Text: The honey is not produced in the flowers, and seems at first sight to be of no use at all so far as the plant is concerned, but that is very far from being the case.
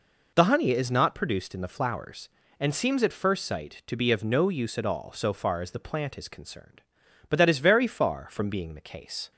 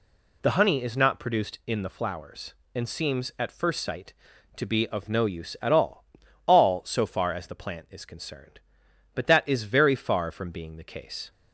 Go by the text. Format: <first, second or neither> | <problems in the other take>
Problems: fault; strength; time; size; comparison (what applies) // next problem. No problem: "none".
first | says "all" twice; at 6.4 s